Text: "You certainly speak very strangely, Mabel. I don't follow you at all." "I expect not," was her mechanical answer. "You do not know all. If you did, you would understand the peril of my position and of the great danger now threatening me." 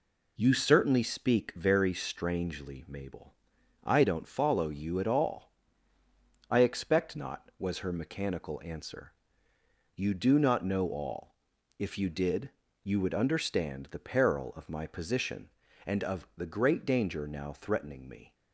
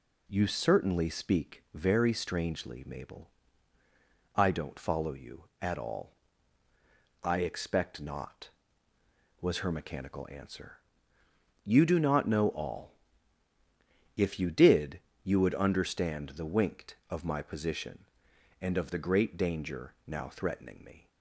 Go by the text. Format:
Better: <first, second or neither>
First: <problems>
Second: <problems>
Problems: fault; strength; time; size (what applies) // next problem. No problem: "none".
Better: first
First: none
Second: says "winked" for "peril"; at 16.4 s